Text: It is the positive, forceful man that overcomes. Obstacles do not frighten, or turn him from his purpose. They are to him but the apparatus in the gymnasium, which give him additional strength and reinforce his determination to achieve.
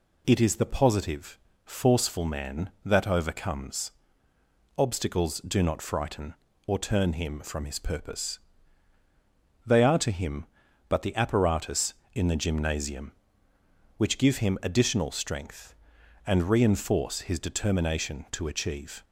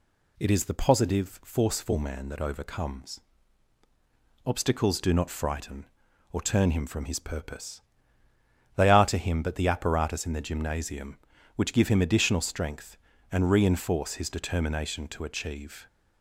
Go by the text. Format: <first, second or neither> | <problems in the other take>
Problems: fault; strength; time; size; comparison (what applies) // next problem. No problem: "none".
neither | none